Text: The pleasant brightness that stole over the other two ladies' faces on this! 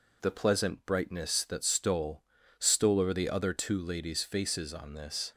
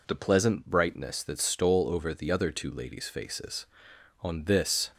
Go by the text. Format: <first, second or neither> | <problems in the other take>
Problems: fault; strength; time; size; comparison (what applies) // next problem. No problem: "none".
second | says "stole" twice; at 2.5 s